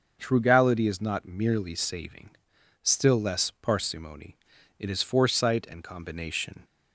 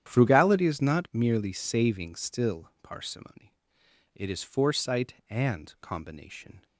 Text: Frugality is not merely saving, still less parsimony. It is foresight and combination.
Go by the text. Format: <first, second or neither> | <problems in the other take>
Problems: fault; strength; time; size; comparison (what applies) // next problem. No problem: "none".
first | starts louder than the rest; strong; until 1.0 s; 10 dB; noticeable in the first // skips "less"; at 2.7 s